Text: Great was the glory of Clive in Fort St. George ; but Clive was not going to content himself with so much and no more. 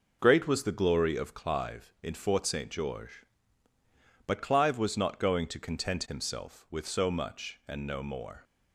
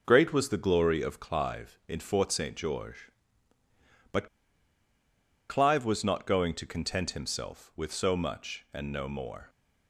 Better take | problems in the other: first | pauses between "but" and "Clive"; at 4.2 s; 1.2 s long

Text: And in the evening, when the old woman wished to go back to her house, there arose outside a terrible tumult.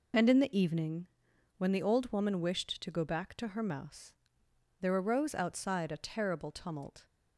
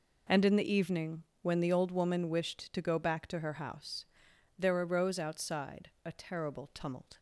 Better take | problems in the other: second | says "mouse" for "house"; at 3.6 s

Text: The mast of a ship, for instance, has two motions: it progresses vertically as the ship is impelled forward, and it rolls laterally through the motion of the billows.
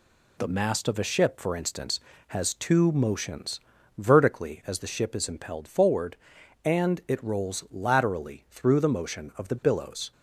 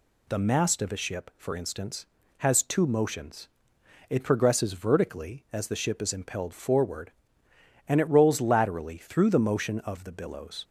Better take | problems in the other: second | skips "it progresses"; at 3.7 s

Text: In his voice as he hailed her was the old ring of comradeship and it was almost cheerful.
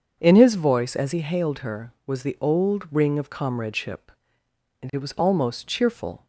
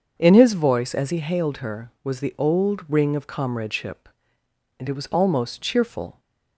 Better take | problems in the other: neither | starts louder than the rest; the same in both

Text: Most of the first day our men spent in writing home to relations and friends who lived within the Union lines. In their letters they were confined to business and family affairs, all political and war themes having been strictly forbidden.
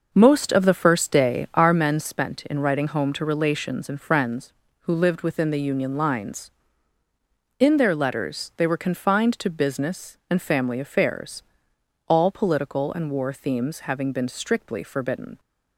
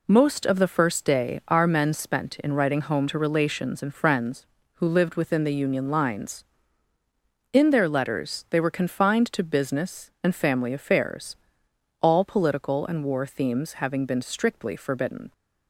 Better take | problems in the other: second | starts louder than the rest; noticeable; until 1.8 s; 6 dB

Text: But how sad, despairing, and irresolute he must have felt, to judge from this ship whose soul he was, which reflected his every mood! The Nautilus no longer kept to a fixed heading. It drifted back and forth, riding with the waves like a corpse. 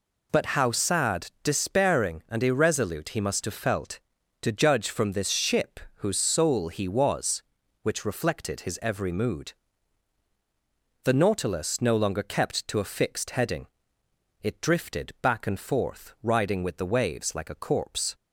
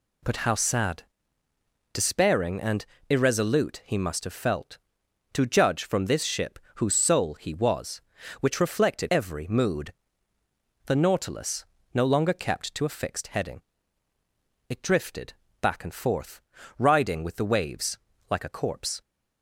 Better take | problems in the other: first | pauses between "and" and "irresolute"; slight; at 2.8 s; 0.24 s long // pauses between "ship" and "whose"; slight; at 6.5 s; 0.18 s long; slight in the first // skips "his"; at 9.0 s // pauses between "Nautilus" and "no"; slight; at 11.6 s; 0.28 s long // pauses between "drifted" and "back"; slight; at 15.3 s; 0.28 s long // pauses between "waves" and "like"; slight; at 17.9 s; 0.30 s long

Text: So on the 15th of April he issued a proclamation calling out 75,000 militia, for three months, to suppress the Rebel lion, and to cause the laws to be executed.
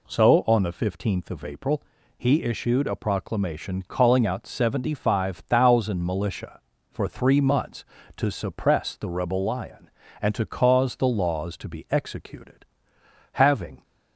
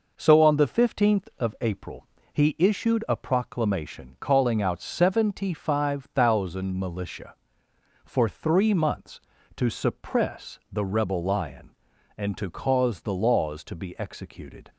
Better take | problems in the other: second | pauses between "April" and "he"; slight; at 1.8 s; 0.36 s long; slight in the second // goes on to say "Having"; from 13.3 s on; 0.50 s long

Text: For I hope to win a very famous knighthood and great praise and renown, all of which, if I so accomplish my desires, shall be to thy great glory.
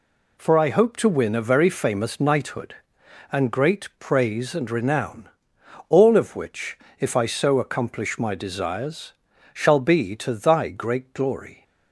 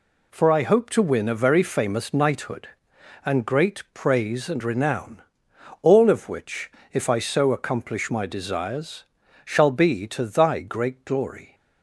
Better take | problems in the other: neither | none

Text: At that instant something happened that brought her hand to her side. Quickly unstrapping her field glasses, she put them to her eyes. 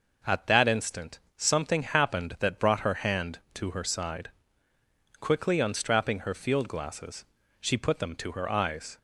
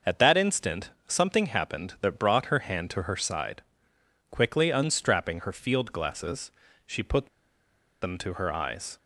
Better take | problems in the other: first | starts louder than the rest; noticeable; until 1.2 s; 6 dB // pauses between "instant" and "something"; slight; at 0.9 s; 0.16 s long; slight in the first // pauses between "put" and "them"; noticeable; at 7.2 s; 0.73 s long

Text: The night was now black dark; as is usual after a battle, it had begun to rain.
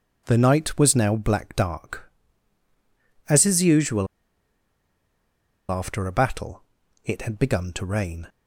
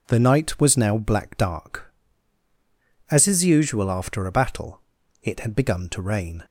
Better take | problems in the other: second | pauses between "usual" and "after"; strong; at 4.0 s; 1.6 s long

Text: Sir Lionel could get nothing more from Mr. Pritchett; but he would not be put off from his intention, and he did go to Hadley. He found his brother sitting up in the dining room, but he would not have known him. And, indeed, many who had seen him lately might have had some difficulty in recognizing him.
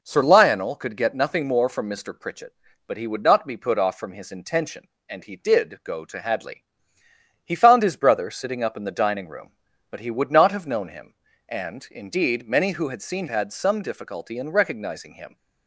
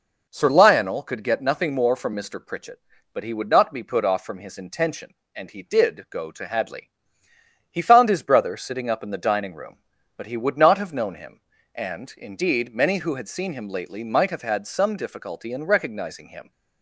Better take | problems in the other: second | skips "him lately might have"; at 13.2 s

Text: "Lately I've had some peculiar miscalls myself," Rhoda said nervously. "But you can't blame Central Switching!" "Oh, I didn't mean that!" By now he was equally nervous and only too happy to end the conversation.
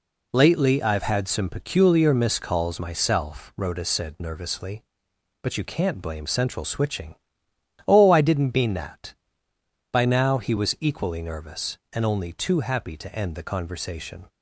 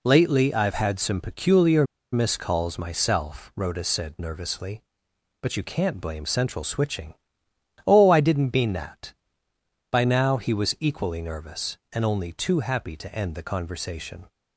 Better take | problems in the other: first | pauses between "peculiar" and "miscalls"; slight; at 1.8 s; 0.29 s long

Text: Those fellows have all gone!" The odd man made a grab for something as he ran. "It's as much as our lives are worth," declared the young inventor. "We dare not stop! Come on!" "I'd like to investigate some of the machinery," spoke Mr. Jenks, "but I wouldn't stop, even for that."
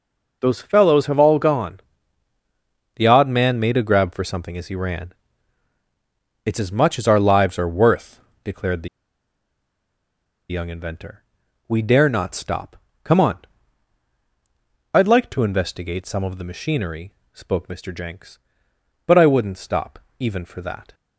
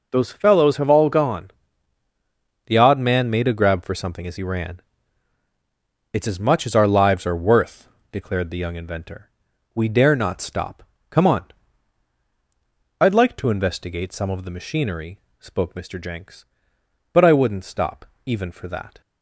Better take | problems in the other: second | pauses between "the" and "young"; strong; at 8.8 s; 1.6 s long

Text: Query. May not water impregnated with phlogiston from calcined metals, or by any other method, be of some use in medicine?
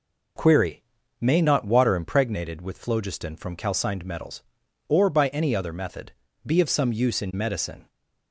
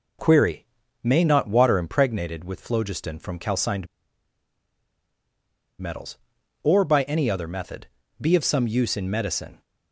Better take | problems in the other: first | pauses between "calcined" and "metals"; strong; at 3.8 s; 1.9 s long

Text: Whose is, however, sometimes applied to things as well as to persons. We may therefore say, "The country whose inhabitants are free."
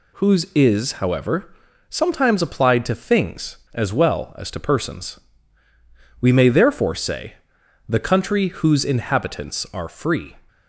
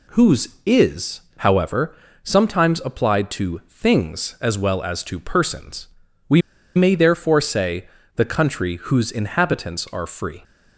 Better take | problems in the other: first | pauses between "We" and "may"; slight; at 6.4 s; 0.35 s long

